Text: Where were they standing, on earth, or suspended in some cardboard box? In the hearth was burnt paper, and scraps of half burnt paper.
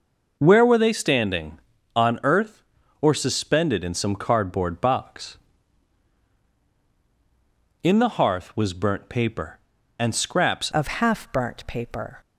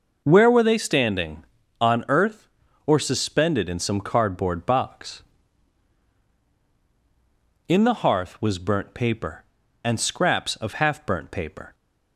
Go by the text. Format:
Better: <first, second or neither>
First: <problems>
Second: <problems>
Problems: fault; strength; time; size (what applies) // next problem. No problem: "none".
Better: second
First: changes voice at "of"; from 10.7 s on; 1.4 s long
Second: none